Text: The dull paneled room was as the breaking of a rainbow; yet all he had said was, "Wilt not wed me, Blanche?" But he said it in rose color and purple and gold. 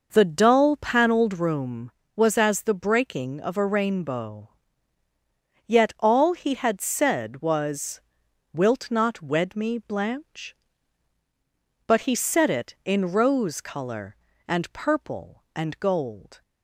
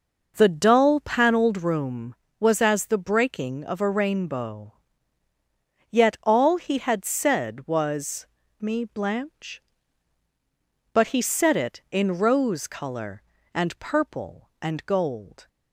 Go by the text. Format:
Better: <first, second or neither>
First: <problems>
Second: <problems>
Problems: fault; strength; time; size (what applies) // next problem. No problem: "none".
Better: first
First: none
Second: skips "Wilt not wed"; at 8.4 s